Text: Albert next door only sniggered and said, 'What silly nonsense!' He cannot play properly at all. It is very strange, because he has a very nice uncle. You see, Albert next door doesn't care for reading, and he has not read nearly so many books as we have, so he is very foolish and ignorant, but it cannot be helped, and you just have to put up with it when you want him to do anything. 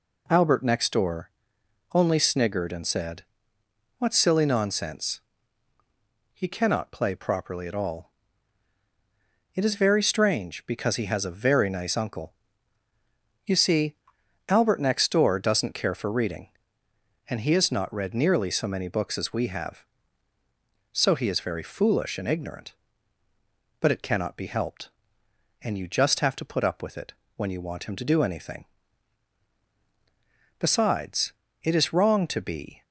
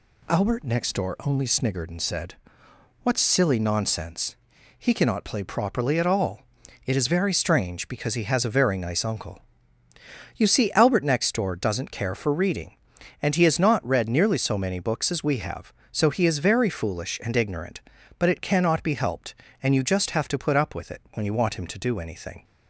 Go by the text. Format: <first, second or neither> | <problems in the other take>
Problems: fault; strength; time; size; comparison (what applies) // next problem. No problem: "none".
second | pauses between "door" and "only"; noticeable; at 1.2 s; 0.64 s long // pauses between "it" and "when"; slight; at 27.1 s; 0.24 s long // goes on to say "Besides it is wrong to be"; strong; from 30.5 s on; 2.2 s long